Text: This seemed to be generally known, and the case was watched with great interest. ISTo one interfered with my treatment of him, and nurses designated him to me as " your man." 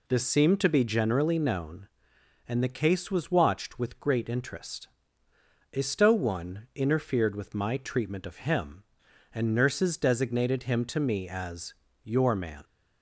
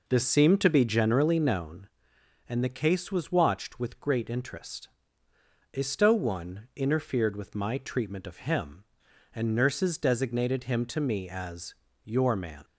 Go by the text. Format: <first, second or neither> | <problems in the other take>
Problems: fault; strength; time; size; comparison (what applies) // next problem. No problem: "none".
first | starts louder than the rest; noticeable; until 1.6 s; 4.5 dB